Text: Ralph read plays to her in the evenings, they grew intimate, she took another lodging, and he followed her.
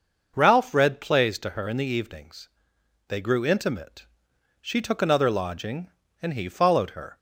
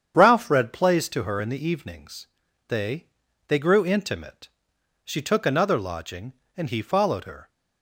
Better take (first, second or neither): first